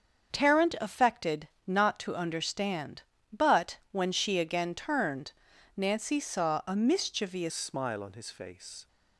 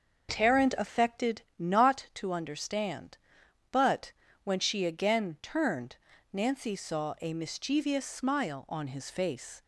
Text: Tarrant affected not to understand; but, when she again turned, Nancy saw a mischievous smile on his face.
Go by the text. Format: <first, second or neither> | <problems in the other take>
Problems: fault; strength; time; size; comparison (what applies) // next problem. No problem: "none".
second | starts louder than the rest; until 1.3 s; 7 dB; also in the second // pauses between "affected" and "not"; slight; at 1.4 s; 0.18 s long; slight in the second // changes voice at "smile"; from 7.5 s on; 1.3 s long